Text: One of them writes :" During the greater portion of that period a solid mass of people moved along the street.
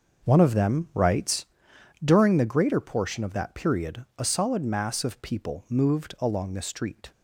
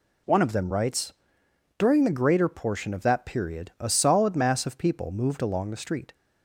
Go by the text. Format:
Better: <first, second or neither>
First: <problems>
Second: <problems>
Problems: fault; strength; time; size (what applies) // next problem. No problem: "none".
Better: second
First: starts louder than the rest; noticeable; until 1.7 s; 6 dB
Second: none